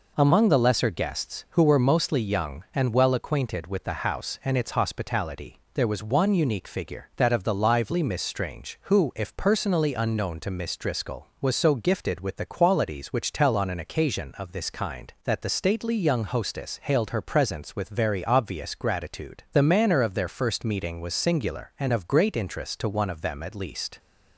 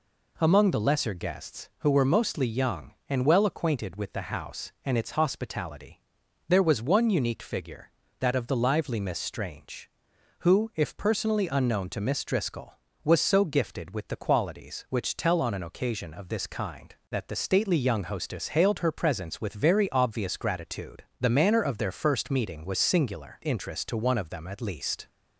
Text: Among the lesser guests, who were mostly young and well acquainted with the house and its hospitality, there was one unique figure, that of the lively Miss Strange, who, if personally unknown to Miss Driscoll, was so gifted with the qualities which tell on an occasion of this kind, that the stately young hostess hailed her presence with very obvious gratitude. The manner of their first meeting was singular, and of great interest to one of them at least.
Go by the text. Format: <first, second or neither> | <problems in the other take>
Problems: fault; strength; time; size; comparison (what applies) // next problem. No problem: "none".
first | skips "and of great"; at 23.4 s